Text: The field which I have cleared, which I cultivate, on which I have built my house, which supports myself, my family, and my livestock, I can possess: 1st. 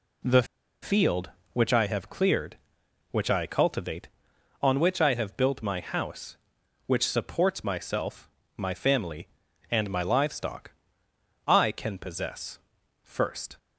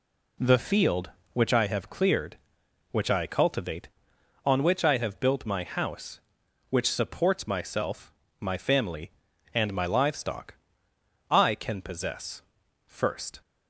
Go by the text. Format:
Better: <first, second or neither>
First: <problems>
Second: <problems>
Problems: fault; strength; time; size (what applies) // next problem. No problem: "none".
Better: second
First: pauses between "The" and "field"; at 0.4 s; 0.38 s long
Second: none